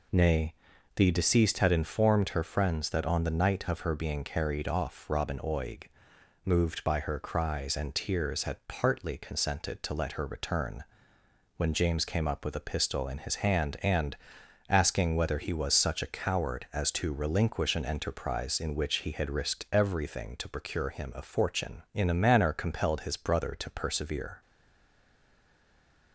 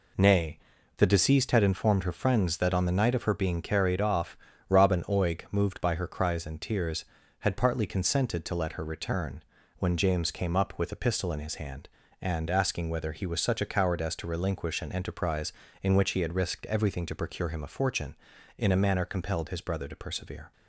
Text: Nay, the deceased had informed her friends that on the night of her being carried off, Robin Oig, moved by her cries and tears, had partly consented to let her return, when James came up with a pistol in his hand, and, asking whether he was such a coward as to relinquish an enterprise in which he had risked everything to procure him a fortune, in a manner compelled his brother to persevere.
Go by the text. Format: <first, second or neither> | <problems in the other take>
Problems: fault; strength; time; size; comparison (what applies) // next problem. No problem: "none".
second | stays silent after the last word; noticeable; from 24.4 s on; 1.7 s long